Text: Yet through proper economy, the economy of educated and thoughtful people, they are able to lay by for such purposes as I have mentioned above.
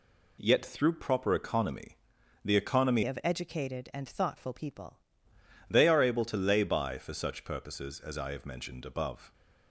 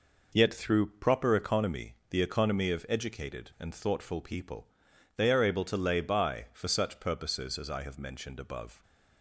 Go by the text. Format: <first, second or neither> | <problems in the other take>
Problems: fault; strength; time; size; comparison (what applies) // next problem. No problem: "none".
second | changes voice from "of" to "people"; from 3.0 to 4.9 s; 1.9 s long